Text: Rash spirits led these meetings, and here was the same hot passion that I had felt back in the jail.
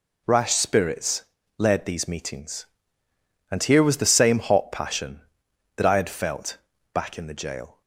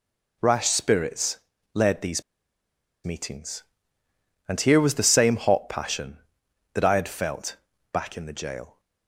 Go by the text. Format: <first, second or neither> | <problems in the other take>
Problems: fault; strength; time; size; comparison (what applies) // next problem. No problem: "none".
first | pauses between "spirits" and "led"; slight; at 1.3 s; 0.36 s long; slight in the first // pauses between "these" and "meetings"; noticeable; at 2.2 s; 0.81 s long // pauses between "felt" and "back"; slight; at 7.5 s; 0.34 s long; slight in the first